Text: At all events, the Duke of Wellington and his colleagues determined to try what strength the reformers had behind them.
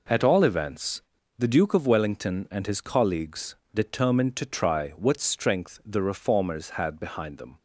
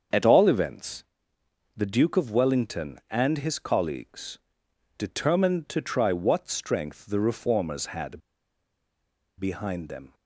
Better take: first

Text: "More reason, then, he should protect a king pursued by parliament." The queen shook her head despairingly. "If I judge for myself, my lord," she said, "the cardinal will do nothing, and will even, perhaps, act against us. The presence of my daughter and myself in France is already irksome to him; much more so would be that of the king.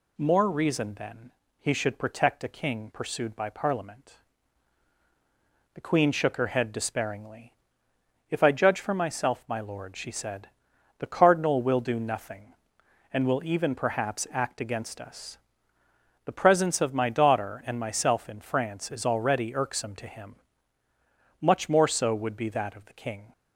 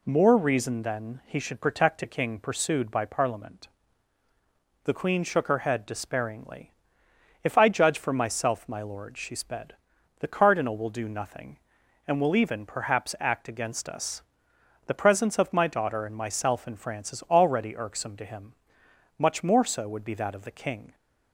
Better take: first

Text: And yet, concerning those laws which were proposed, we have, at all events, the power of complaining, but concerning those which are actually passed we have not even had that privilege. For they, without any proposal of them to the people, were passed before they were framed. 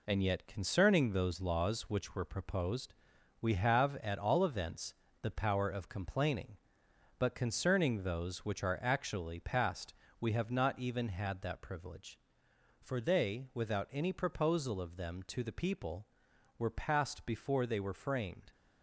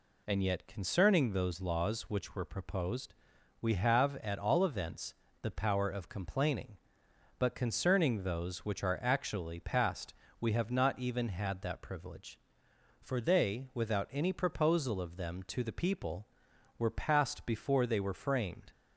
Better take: second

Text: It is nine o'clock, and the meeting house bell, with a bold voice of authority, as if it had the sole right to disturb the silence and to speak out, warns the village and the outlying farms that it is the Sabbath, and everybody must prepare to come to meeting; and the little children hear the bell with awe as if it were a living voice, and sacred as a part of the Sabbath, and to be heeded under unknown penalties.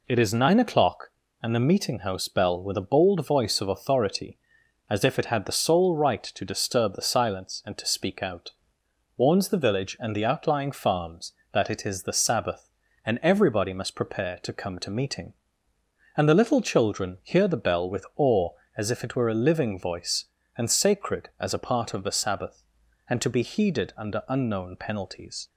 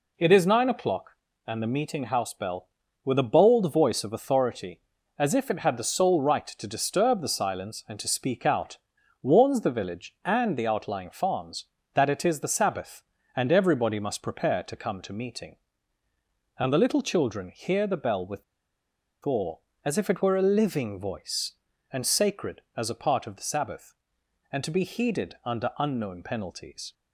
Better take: first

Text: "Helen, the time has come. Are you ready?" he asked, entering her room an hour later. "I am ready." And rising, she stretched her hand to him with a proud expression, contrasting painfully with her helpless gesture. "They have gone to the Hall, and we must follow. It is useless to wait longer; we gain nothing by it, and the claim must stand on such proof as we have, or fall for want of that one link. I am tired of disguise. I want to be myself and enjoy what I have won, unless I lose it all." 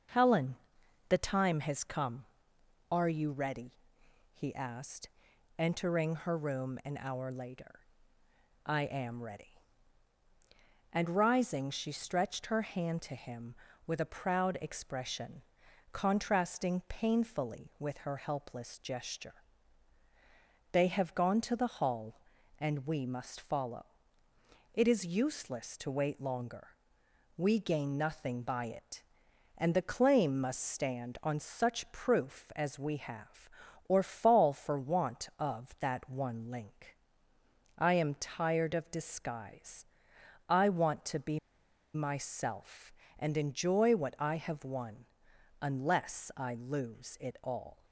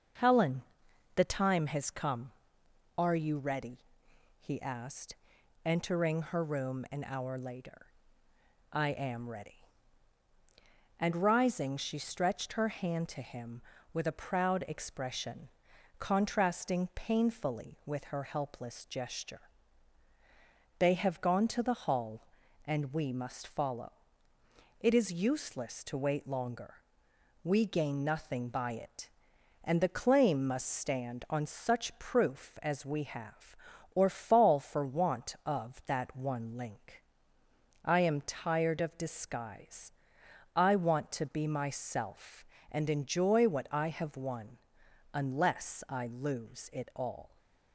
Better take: second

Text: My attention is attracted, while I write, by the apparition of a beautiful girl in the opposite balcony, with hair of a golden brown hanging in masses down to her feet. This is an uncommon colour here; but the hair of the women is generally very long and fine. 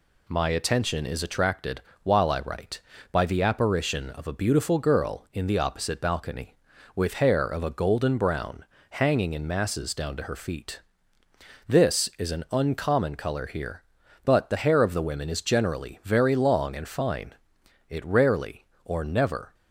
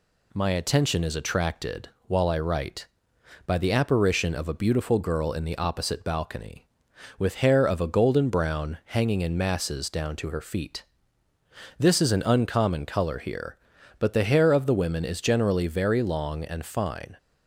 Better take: second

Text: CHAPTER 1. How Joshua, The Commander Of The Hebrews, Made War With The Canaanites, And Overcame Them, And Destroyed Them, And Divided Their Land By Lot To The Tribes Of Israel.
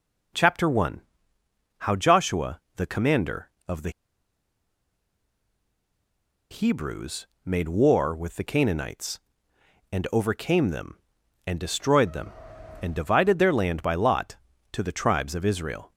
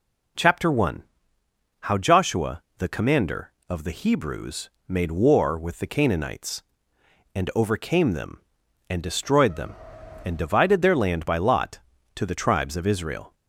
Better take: second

